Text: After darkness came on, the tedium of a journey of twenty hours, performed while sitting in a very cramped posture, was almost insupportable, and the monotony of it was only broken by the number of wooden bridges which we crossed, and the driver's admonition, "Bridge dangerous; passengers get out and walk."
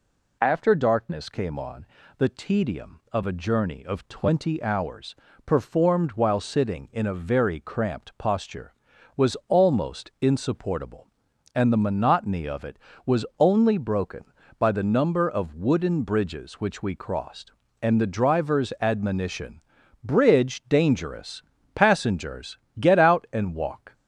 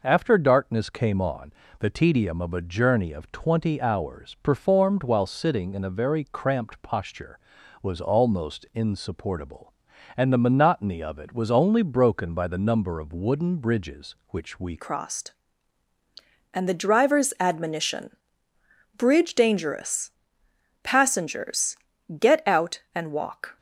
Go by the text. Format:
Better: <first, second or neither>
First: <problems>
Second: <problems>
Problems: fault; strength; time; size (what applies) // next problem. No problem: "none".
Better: first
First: pauses between "passengers" and "get"; slight; at 22.5 s; 0.20 s long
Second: changes voice at "crossed"; from 14.7 s on; 8.8 s long // pauses between "passengers" and "get"; at 21.7 s; 0.42 s long